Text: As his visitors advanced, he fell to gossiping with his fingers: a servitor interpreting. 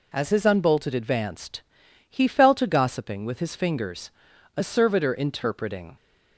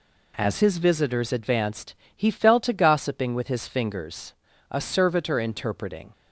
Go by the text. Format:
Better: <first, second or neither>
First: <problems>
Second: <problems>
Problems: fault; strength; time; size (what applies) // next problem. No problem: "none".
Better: second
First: says "unbolted" for "visitors"; at 0.4 s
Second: none